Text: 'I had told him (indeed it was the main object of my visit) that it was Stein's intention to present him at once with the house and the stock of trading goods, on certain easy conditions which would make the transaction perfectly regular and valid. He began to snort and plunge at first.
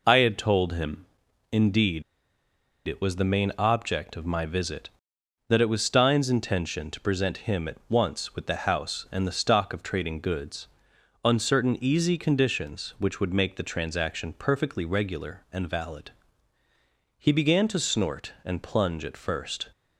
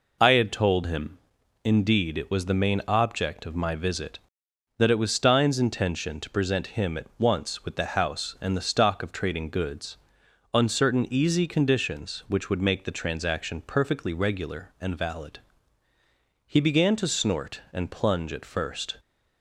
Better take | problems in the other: second | pauses between "indeed" and "it"; noticeable; at 2.0 s; 0.84 s long

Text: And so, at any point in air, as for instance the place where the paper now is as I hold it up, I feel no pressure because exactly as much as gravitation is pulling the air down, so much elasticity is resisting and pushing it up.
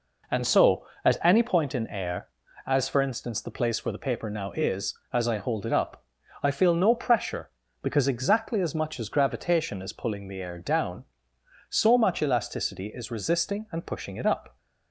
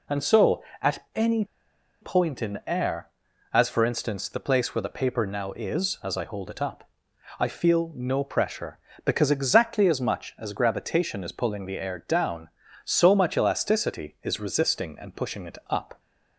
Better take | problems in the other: first | pauses between "any" and "point"; noticeable; at 1.4 s; 0.56 s long

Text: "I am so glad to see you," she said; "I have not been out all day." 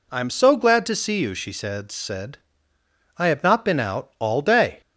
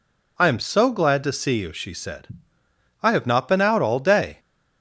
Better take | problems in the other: second | says "said" twice; at 1.9 s

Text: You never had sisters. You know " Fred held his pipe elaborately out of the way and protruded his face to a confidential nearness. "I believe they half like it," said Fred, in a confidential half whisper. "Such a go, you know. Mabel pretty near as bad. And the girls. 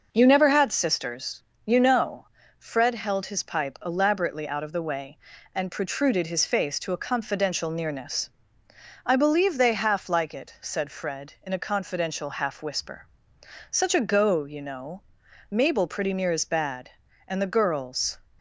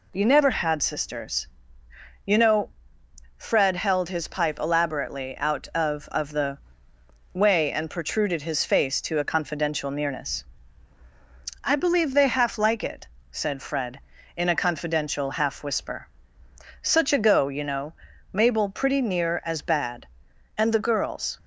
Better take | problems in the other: first | says "of" twice; at 6.0 s // pauses between "the" and "way"; noticeable; at 6.5 s; 0.74 s long

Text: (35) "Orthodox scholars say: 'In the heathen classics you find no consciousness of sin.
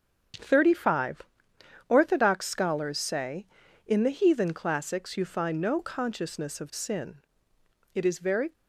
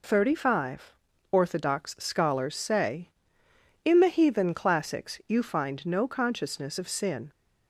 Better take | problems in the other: second | starts louder than the rest; strong; until 1.9 s; 7.5 dB // goes on to say "It is very"; from 7.9 s on; 0.58 s long

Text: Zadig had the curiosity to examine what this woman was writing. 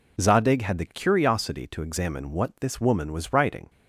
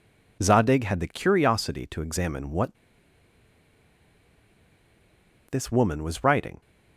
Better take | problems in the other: first | pauses between "what" and "this"; strong; at 2.7 s; 2.7 s long

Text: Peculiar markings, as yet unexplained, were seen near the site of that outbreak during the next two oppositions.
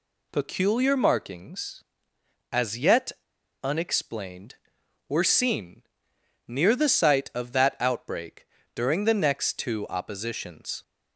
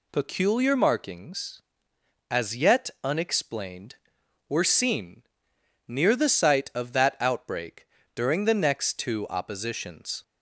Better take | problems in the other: second | pauses between "yet" and "unexplained"; noticeable; at 3.1 s; 0.50 s long // pauses between "seen" and "near"; noticeable; at 5.8 s; 0.66 s long; noticeable in the second // pauses between "outbreak" and "during"; slight; at 8.4 s; 0.26 s long; slight in the second

